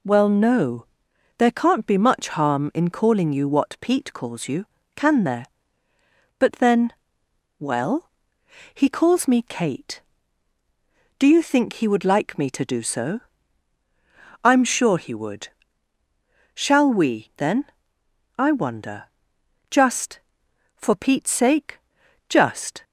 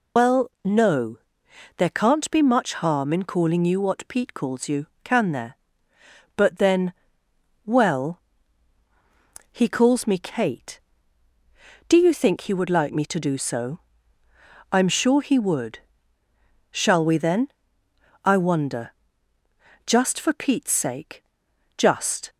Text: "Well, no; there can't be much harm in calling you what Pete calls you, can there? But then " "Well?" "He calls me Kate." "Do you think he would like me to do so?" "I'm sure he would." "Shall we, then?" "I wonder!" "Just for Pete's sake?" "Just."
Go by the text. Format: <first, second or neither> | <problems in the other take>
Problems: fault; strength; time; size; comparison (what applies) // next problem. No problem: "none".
first | loses the start of "Well"; at 0.1 s; 65 ms